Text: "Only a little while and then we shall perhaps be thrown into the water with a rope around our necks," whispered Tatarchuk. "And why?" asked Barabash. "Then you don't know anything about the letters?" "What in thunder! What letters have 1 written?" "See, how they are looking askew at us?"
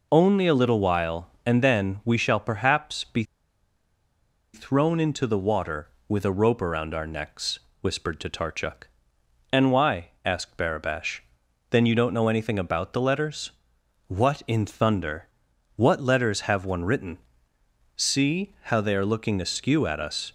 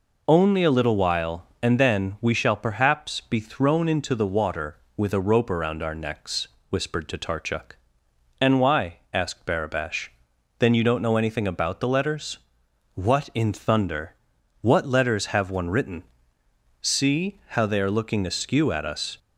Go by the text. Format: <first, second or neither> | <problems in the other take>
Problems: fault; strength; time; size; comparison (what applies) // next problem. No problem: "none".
second | pauses between "be" and "thrown"; strong; at 3.2 s; 1.3 s long